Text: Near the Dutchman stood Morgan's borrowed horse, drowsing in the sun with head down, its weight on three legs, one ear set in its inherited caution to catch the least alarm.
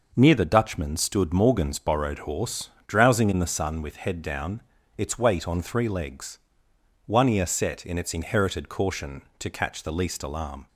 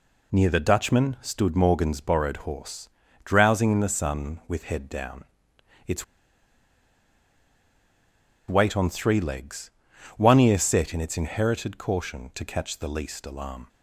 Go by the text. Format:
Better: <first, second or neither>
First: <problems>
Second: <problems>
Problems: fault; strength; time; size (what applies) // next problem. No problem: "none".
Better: first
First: none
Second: pauses between "its" and "weight"; strong; at 6.0 s; 2.4 s long